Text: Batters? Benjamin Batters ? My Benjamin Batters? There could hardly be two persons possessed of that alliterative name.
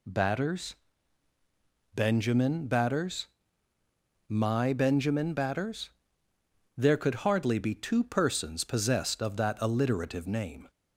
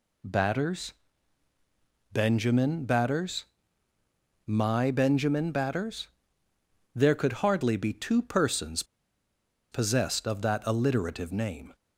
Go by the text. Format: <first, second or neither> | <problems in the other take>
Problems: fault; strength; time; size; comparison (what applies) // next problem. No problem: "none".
first | pauses between "persons" and "possessed"; noticeable; at 8.8 s; 0.90 s long